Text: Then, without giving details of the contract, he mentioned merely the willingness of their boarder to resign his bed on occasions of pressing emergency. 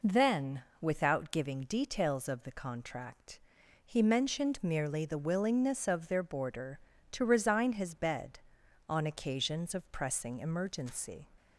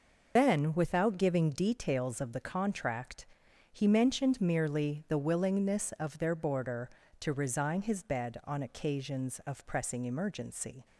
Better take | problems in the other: first | loses the start of "Then"; at 0.3 s; 105 ms

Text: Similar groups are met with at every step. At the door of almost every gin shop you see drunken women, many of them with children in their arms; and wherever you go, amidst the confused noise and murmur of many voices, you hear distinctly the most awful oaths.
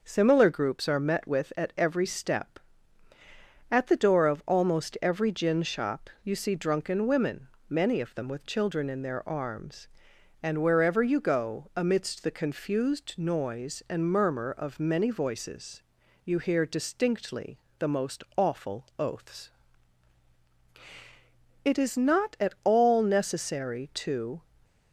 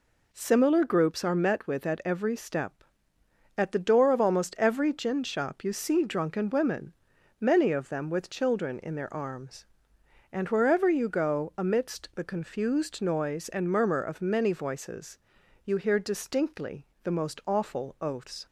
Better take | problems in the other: second | pauses between "distinctly" and "the"; slight; at 17.5 s; 0.20 s long; slight in the second // goes on to say "It is not at all necessary to"; strong; from 21.6 s on; 2.7 s long // stays silent after the last word; slight; from 24.4 s on; 0.5 s long

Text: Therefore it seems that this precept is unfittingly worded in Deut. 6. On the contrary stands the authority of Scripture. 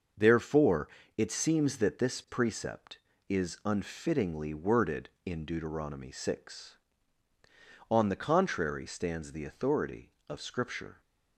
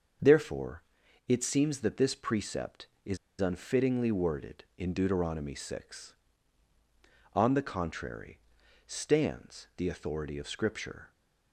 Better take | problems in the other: first | starts louder than the rest; until 1.6 s; 6.5 dB; also in the first // pauses between "Therefore" and "it"; noticeable; at 0.8 s; 0.46 s long; slight in the first // pauses between "is" and "unfittingly"; slight; at 3.1 s; 0.23 s long // pauses between "contrary" and "stands"; noticeable; at 8.3 s; 0.48 s long

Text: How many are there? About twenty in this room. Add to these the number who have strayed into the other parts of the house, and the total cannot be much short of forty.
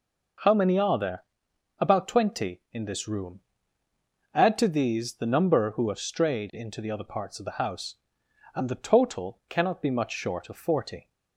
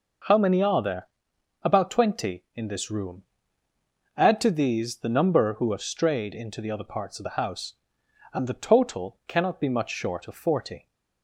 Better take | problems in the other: neither | none

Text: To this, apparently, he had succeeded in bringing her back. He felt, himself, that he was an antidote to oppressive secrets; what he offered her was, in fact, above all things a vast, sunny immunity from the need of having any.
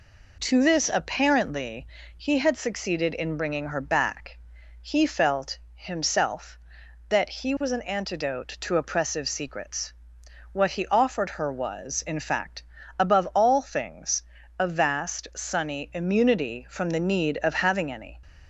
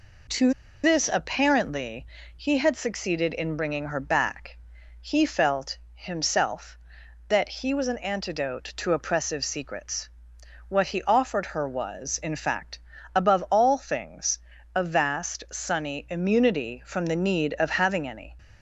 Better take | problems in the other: first | pauses between "To" and "this"; slight; at 0.5 s; 0.32 s long // pauses between "things" and "a"; slight; at 14.3 s; 0.36 s long; slight in the first

